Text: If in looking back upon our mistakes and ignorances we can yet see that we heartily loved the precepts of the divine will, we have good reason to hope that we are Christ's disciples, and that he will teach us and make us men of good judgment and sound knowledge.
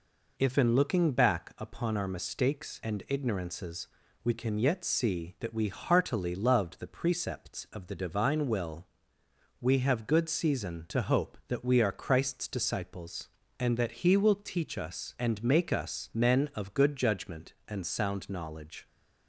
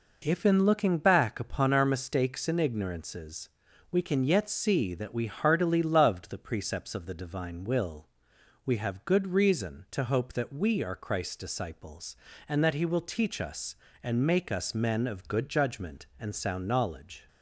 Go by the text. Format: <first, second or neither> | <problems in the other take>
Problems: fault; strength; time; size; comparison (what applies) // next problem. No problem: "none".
second | pauses between "ignorances" and "we"; at 3.8 s; 0.38 s long; also in the second // says "season" for "reason"; at 10.3 s